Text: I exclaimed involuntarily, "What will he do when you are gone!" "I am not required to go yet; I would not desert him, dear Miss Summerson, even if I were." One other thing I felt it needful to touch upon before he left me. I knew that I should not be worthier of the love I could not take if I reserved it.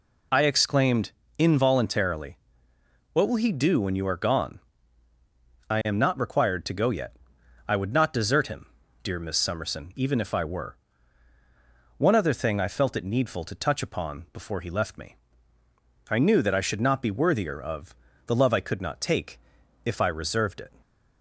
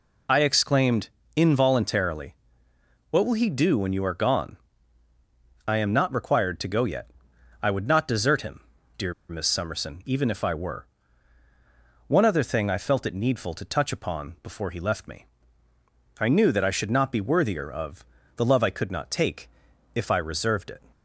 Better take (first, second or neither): first